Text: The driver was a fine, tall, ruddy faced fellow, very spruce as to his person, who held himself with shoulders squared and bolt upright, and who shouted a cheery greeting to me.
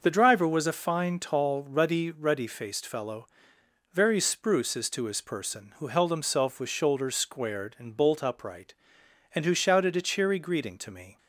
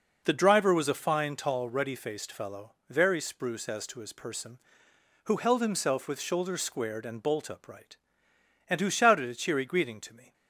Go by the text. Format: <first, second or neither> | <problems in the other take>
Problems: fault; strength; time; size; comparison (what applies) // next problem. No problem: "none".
second | starts louder than the rest; noticeable; until 1.0 s; 6 dB // says "ruddy" twice; at 2.0 s